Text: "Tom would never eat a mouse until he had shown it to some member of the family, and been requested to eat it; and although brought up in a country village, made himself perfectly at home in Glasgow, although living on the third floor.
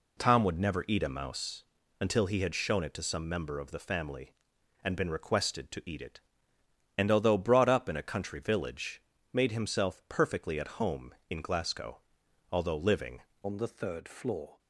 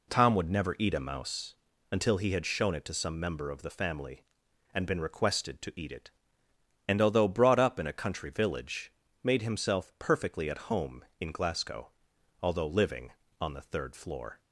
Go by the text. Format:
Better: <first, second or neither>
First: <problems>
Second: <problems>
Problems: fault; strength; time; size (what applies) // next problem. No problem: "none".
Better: second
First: pauses between "mouse" and "until"; slight; at 1.6 s; 0.36 s long // changes voice at "on"; from 13.4 s on; 1.1 s long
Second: pauses between "mouse" and "until"; slight; at 1.5 s; 0.36 s long